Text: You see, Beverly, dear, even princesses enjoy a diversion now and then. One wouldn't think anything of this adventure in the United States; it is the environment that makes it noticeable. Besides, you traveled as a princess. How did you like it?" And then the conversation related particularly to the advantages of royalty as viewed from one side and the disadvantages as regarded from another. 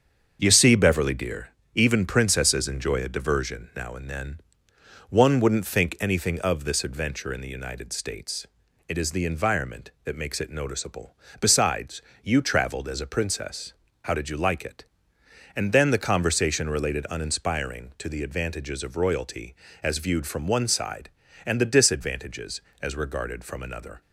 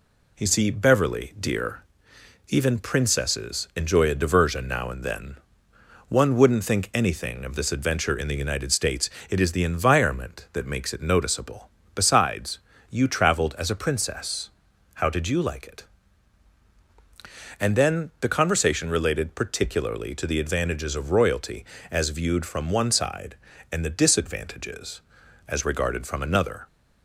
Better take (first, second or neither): second